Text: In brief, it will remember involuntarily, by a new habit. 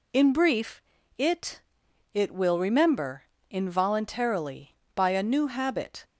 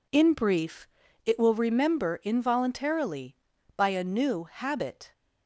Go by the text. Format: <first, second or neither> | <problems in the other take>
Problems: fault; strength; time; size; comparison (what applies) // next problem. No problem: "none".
second | says "it" twice; at 2.1 s // pauses between "remember" and "involuntarily"; slight; at 3.2 s; 0.22 s long